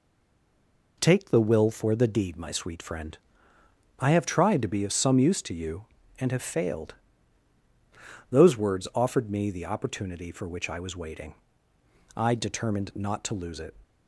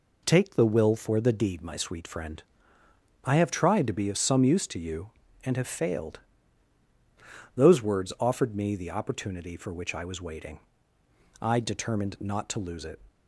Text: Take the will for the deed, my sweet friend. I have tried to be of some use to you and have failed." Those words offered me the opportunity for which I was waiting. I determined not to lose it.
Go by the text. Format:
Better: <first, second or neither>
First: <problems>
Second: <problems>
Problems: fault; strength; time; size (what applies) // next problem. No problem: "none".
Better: second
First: stays silent before the first word; until 0.9 s; 0.9 s long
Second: none